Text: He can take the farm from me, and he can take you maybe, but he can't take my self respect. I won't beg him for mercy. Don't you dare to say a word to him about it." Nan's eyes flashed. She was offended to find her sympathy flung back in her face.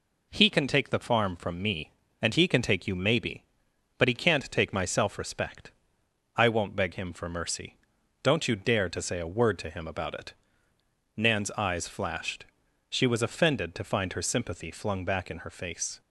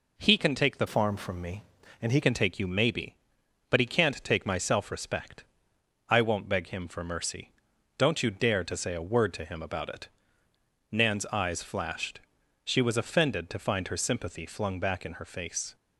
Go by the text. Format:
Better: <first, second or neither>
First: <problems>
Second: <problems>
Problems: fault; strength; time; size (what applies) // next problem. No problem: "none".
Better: first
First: none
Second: changes voice from "farm" to "he"; from 0.8 to 2.2 s; 1.4 s long